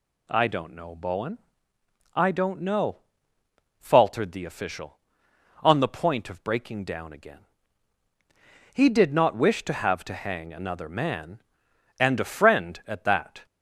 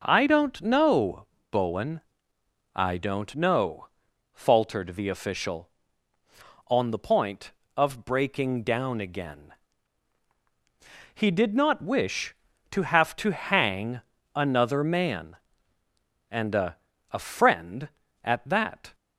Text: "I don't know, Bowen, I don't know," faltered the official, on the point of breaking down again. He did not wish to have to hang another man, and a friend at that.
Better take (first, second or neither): first